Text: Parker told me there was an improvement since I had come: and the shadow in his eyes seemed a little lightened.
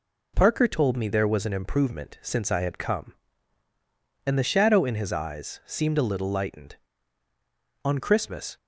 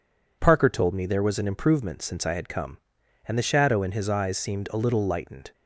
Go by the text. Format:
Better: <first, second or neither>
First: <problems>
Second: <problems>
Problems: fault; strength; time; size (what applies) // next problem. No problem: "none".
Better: second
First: goes on to say "On Christmas"; noticeable; from 7.8 s on; 0.72 s long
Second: none